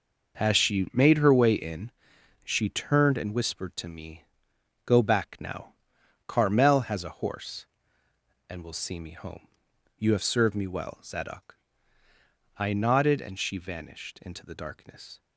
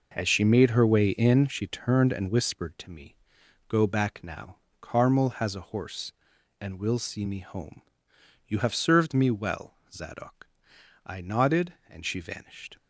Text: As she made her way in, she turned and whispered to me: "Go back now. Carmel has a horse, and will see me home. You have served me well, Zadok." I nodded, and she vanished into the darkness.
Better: first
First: none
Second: stops before "into the darkness"; at 12.7 s

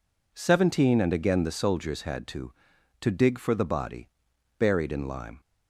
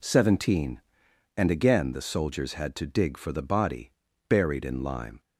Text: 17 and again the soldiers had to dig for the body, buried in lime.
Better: second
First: says "to" twice; at 3.0 s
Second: none

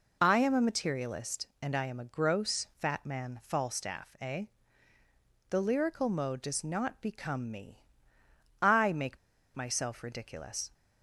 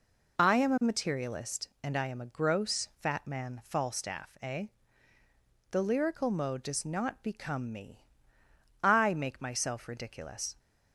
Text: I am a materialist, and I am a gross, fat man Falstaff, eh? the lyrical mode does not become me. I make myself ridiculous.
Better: second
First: pauses between "make" and "myself"; at 9.1 s; 0.38 s long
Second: none

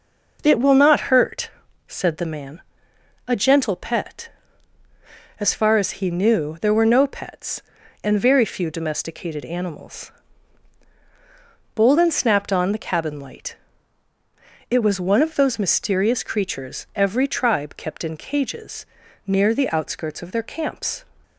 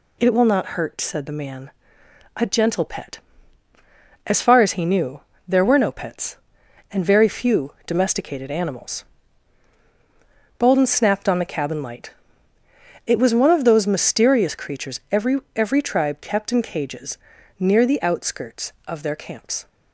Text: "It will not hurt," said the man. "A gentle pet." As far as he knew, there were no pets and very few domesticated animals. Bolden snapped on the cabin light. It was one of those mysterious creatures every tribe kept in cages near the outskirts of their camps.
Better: first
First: pauses between "cages" and "near"; at 18.8 s; 0.40 s long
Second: says "every" twice; at 15.5 s // pauses between "cages" and "near"; at 17.1 s; 0.40 s long

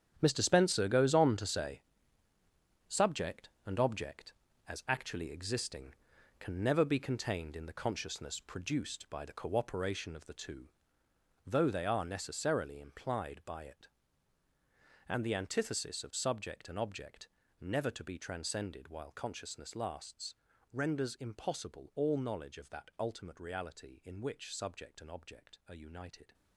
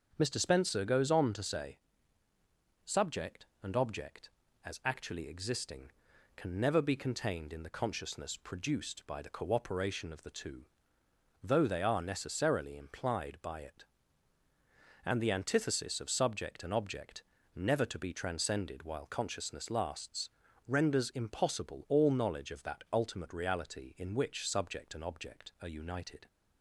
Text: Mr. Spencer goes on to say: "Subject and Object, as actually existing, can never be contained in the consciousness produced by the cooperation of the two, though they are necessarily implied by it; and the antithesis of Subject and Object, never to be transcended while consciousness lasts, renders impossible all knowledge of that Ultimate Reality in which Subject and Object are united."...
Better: second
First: gets quieter; strong; throughout; 12.5 dB // starts louder than the rest; strong; until 1.2 s; 9 dB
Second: starts louder than the rest; until 1.1 s; 7 dB

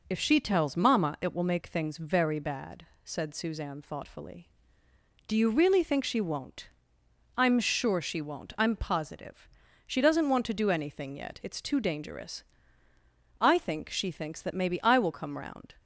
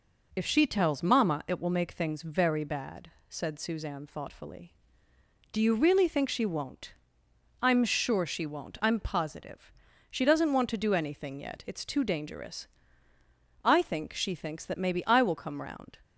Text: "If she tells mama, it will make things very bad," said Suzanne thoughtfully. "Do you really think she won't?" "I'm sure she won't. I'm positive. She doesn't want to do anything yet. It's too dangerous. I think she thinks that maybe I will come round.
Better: neither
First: none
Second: none

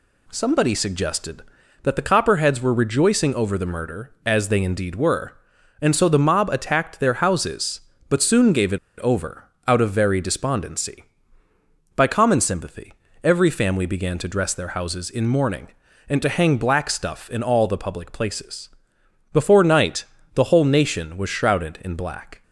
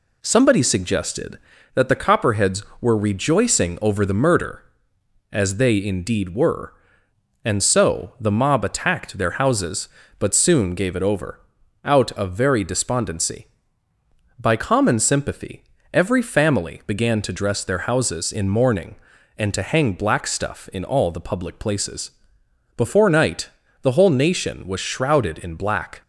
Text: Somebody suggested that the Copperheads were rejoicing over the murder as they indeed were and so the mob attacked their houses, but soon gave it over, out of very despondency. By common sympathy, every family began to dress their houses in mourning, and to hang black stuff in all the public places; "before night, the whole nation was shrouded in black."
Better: second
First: pauses between "it" and "over"; slight; at 8.7 s; 0.19 s long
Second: none

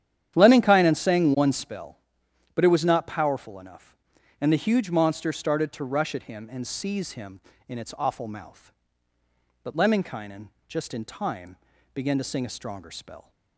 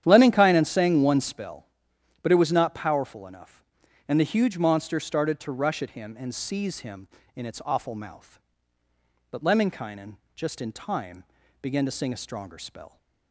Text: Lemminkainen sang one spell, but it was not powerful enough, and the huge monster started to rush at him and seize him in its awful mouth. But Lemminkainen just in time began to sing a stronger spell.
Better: neither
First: starts louder than the rest; strong; until 1.3 s; 10 dB // pauses between "Lemminkainen" and "just"; slight; at 10.4 s; 0.20 s long // pauses between "time" and "began"; at 11.5 s; 0.38 s long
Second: starts louder than the rest; strong; until 1.0 s; 10 dB // pauses between "Lemminkainen" and "just"; slight; at 10.1 s; 0.20 s long // pauses between "time" and "began"; at 11.2 s; 0.38 s long

